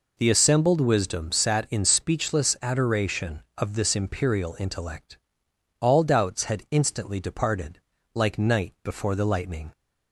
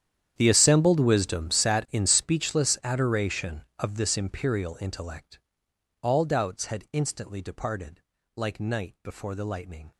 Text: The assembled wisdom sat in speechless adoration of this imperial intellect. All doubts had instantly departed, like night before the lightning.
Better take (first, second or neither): first